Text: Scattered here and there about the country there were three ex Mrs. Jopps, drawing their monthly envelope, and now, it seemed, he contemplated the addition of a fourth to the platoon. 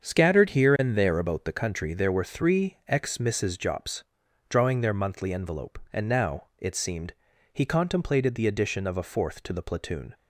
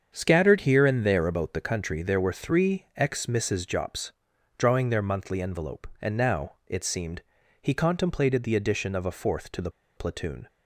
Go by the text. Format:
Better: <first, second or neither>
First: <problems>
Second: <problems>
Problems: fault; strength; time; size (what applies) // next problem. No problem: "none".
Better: first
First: starts louder than the rest; until 1.0 s; 7 dB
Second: starts louder than the rest; strong; until 1.1 s; 7 dB // pauses between "the" and "platoon"; slight; at 9.7 s; 0.26 s long